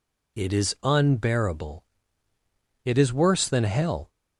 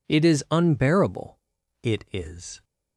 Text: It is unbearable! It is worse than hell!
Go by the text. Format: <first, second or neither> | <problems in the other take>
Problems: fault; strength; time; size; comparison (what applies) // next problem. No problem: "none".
first | stops before "worse than hell"; at 2.6 s